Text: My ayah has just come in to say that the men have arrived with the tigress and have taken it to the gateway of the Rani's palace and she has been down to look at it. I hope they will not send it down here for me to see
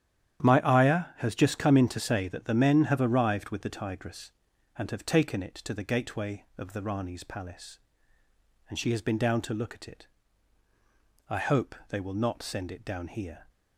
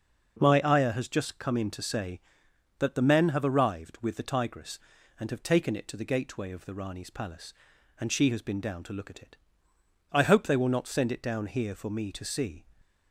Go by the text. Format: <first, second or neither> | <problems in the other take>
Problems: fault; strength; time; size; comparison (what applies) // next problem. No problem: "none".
second | starts louder than the rest; strong; until 1.5 s; 10 dB // stops before "for me to see"; at 13.4 s